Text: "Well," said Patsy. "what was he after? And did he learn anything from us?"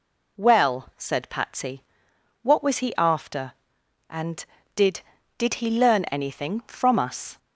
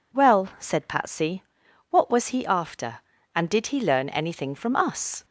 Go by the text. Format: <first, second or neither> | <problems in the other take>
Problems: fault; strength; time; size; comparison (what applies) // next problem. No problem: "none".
second | says "did" twice; at 5.3 s